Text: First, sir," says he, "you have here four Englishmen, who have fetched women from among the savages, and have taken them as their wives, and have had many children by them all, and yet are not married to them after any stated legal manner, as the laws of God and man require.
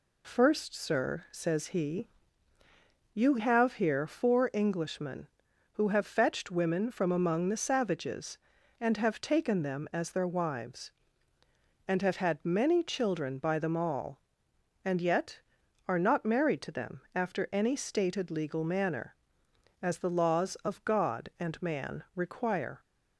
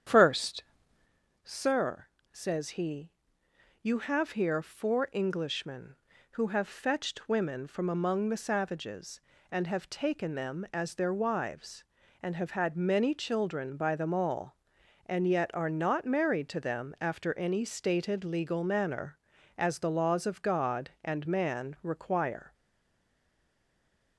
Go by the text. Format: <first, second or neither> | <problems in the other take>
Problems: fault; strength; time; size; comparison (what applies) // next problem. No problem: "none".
first | starts louder than the rest; strong; until 1.8 s; 9 dB // stays silent after the last word; noticeable; from 22.5 s on; 1.6 s long